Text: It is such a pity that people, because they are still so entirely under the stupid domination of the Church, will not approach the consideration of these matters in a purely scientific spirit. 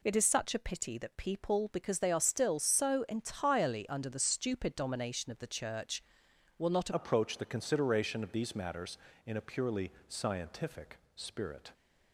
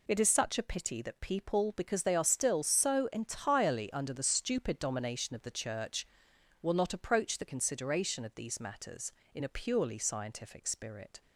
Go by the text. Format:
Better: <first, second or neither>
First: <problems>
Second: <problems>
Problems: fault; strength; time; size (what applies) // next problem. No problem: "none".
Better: second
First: changes voice at "approach"; from 6.9 s on; 4.8 s long // pauses between "purely" and "scientific"; slight; at 9.9 s; 0.16 s long // pauses between "scientific" and "spirit"; slight; at 10.9 s; 0.18 s long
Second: none